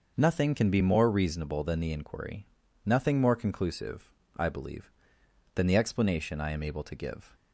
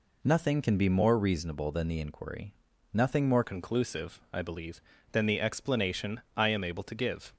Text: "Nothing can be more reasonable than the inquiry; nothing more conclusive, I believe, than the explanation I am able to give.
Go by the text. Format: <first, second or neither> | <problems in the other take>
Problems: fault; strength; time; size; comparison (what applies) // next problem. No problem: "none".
first | changes voice at "conclusive"; from 3.4 s on; 3.9 s long